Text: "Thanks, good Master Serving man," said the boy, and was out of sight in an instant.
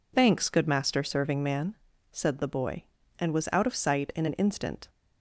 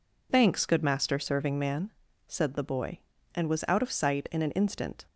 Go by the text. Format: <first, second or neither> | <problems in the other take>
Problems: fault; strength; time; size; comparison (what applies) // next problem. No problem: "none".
neither | none